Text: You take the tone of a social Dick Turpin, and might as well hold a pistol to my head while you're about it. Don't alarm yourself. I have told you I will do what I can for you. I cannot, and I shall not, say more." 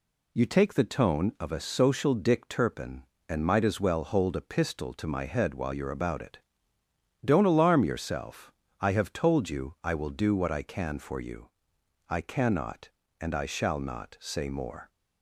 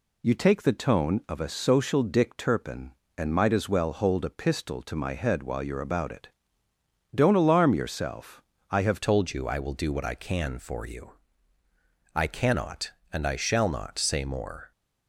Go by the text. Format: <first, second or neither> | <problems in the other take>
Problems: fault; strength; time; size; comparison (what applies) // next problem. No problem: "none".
first | changes voice at "told"; from 9.0 s on; 5.7 s long